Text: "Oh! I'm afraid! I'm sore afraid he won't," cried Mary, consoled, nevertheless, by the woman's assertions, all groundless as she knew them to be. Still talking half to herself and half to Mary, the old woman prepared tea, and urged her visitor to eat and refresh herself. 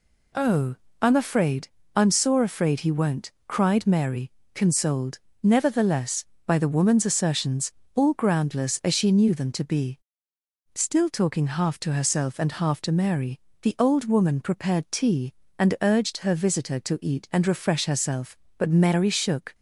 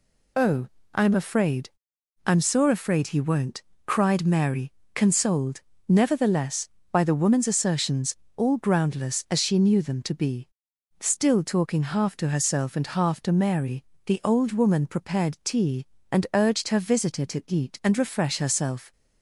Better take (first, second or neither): second